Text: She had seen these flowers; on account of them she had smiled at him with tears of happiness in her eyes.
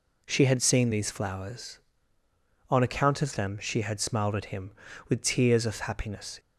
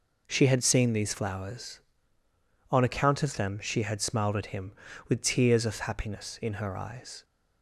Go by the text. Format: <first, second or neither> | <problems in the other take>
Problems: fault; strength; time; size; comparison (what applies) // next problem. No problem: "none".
second | stops before "in her eyes"; at 6.3 s